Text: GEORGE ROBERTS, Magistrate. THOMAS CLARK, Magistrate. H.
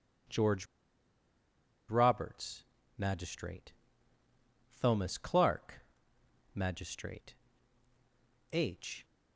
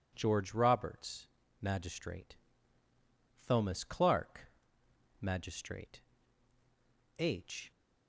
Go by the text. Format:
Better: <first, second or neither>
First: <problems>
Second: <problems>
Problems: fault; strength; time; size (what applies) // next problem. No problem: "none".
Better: second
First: pauses between "GEORGE" and "ROBERTS"; at 0.6 s; 1.2 s long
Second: none